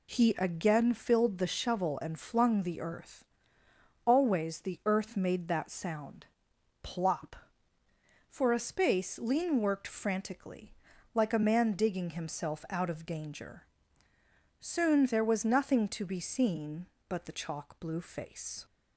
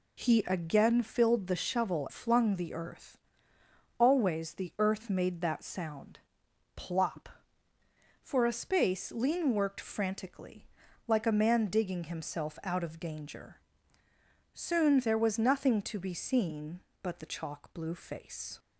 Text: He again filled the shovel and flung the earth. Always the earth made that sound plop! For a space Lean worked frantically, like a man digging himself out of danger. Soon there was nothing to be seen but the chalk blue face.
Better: first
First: pauses between "sound" and "plop"; noticeable; at 6.2 s; 0.56 s long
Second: skips "and"; at 2.0 s // pauses between "sound" and "plop"; noticeable; at 6.1 s; 0.56 s long

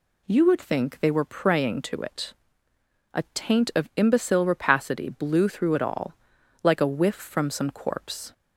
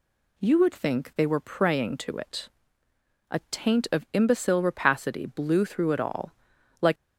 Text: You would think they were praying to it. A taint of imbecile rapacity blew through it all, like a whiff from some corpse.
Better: first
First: none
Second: stops before "a whiff from some corpse"; at 6.9 s

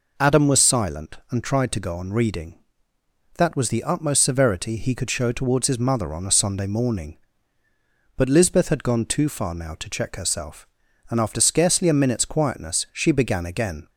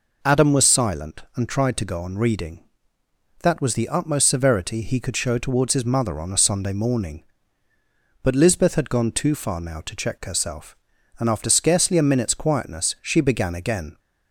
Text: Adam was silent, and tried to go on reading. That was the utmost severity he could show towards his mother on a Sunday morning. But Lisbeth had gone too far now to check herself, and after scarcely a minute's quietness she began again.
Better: neither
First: none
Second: none

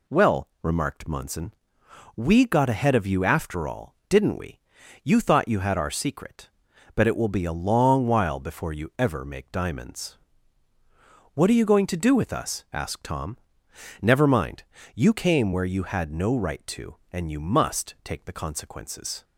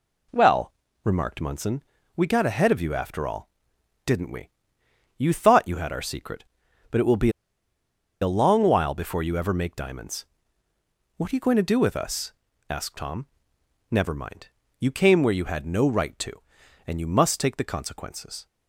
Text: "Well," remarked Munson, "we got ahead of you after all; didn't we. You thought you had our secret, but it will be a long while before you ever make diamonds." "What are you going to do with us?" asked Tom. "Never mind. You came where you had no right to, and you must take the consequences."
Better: first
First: none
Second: pauses between "be" and "a"; noticeable; at 7.3 s; 0.91 s long

